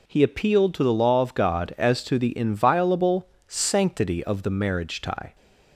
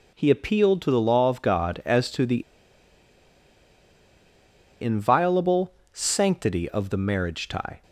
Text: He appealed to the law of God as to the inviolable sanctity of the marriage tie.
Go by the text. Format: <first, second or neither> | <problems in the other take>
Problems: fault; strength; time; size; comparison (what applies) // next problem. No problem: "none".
first | pauses between "the" and "inviolable"; strong; at 2.4 s; 2.3 s long // pauses between "inviolable" and "sanctity"; slight; at 5.7 s; 0.20 s long; slight in the first